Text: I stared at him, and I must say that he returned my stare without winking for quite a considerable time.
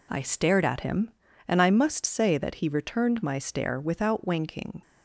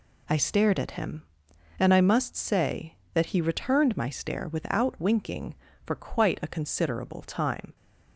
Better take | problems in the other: second | stops before "for quite a considerable time"; at 4.8 s

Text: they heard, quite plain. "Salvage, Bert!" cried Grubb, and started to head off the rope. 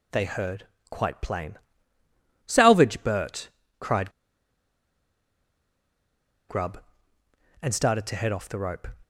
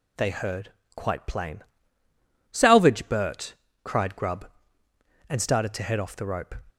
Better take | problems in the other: second | pauses between "cried" and "Grubb"; strong; at 4.1 s; 2.3 s long

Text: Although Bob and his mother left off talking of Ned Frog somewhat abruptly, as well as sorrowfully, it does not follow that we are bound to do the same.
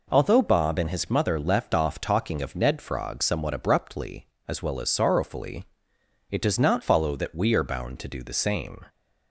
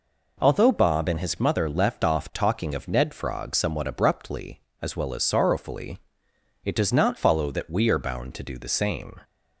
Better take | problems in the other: neither | none

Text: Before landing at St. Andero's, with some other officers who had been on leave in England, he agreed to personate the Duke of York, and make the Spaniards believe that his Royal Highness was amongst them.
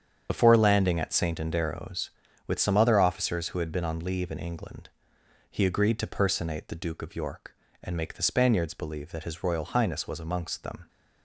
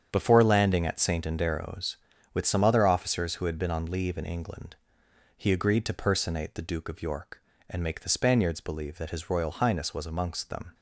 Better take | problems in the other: second | loses the start of "Before"; at 0.2 s; 45 ms // starts louder than the rest; strong; until 1.3 s; 8 dB; strong in the second

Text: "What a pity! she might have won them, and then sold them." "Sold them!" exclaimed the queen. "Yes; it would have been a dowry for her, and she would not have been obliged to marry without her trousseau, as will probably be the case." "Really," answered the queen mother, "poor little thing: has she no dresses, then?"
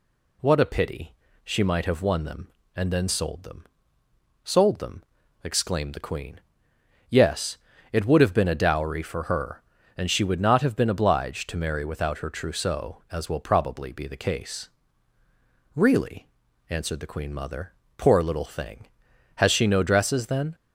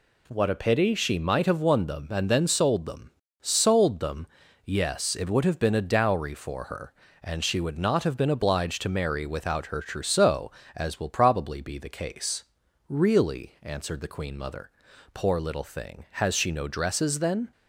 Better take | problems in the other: first | skips "exclaimed the queen"; at 4.4 s

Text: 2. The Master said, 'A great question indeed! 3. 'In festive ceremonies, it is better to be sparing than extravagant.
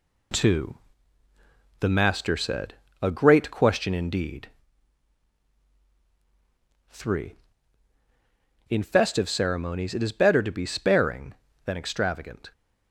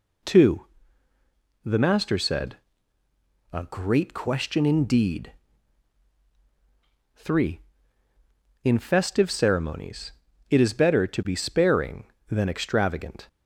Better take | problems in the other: second | gets quieter; noticeable; throughout; 4.5 dB

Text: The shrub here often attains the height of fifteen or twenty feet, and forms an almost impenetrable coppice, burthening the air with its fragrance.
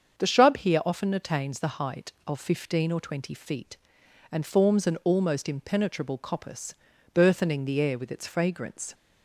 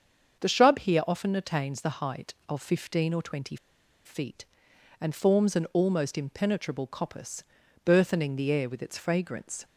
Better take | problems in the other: first | starts louder than the rest; until 1.4 s; 7 dB; also in the first // pauses between "twenty" and "feet"; noticeable; at 3.5 s; 0.49 s long

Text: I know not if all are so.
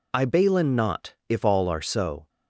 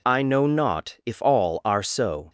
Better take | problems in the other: second | says "balin" for "know"; at 0.2 s // pauses between "not" and "if"; slight; at 1.1 s; 0.16 s long

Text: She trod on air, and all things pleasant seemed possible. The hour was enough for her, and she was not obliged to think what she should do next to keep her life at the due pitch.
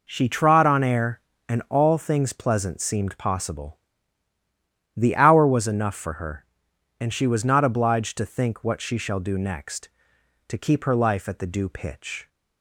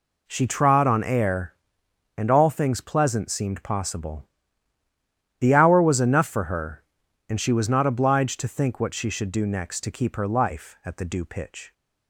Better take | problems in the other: second | says "shall" for "should"; at 8.9 s

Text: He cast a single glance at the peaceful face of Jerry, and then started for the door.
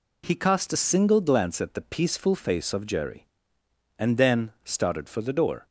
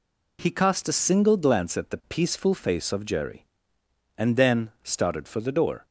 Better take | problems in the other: neither | none

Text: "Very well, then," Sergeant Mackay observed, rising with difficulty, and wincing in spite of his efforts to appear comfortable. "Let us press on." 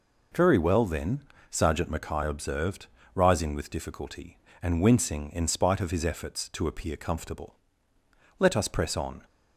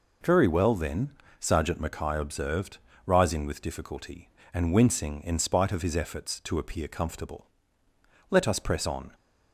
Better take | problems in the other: neither | none

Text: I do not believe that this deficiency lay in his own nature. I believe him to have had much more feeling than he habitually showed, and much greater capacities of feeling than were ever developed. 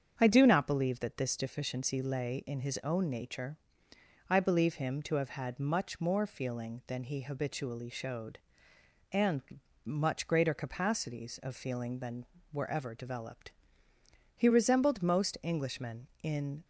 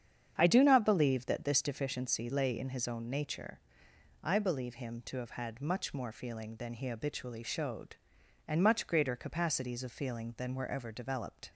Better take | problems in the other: second | starts louder than the rest; strong; until 1.1 s; 7 dB; strong in the second // pauses between "and" and "much"; at 9.4 s; 0.42 s long // goes on to say "He resembled most Englishmen in"; strong; from 14.3 s on; 2.3 s long

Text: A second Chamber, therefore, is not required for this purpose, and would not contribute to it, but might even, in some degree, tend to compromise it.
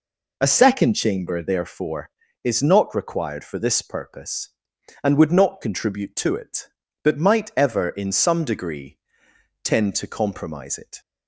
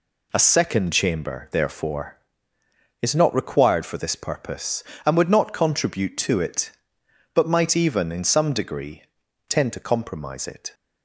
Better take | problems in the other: second | says "ever" for "even"; at 7.5 s

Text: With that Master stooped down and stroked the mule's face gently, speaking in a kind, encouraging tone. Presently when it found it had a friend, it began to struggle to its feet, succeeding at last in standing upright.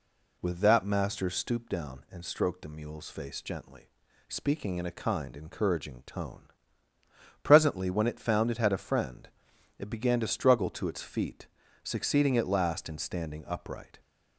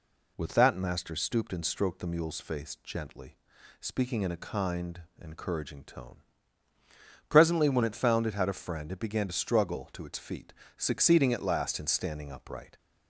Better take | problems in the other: first | skips "down"; at 1.5 s

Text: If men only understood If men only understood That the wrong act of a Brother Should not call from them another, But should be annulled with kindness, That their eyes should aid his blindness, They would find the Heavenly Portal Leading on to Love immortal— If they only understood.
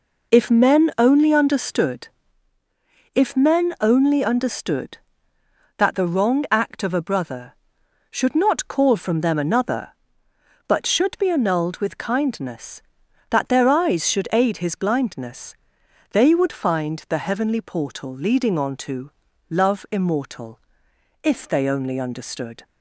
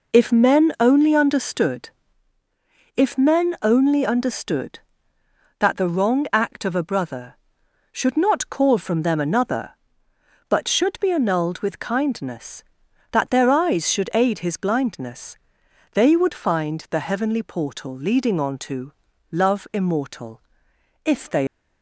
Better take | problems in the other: first | pauses between "understood" and "If"; at 1.8 s; 1.0 s long; also in the first // pauses between "to" and "Love"; slight; at 18.9 s; 0.36 s long; slight in the first // stops before "only understood"; at 21.4 s

